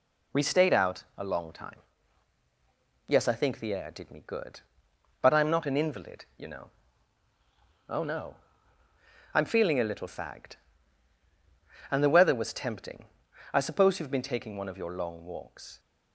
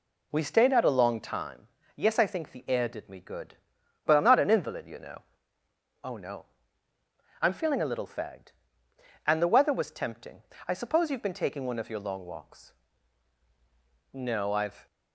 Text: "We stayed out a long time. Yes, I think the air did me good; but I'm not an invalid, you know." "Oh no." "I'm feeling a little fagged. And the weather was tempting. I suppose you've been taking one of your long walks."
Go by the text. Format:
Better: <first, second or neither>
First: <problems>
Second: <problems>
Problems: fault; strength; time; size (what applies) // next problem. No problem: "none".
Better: first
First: none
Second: goes on to say "No I've"; noticeable; from 14.1 s on; 0.74 s long